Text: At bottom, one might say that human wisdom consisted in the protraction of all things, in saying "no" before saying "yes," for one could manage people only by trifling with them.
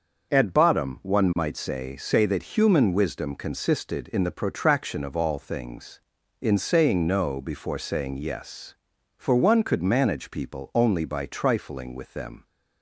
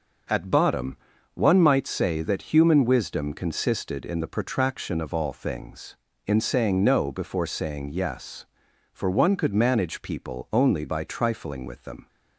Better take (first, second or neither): second